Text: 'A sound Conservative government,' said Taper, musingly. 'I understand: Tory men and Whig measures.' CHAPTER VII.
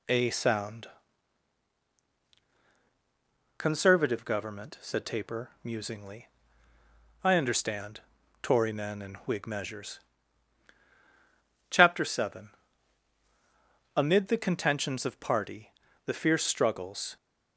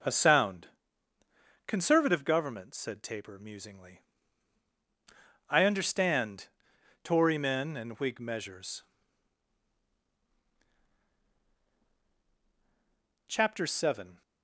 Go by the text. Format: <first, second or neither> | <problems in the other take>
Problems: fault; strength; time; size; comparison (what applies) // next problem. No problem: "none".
second | pauses between "sound" and "Conservative"; strong; at 0.8 s; 2.6 s long; also in the second // goes on to say "Amid the contentions of party the fierce struggles"; strong; from 13.9 s on; 3.2 s long